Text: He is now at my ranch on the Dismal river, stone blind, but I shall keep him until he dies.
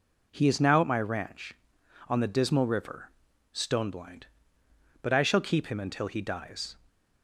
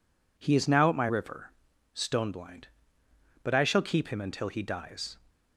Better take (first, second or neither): first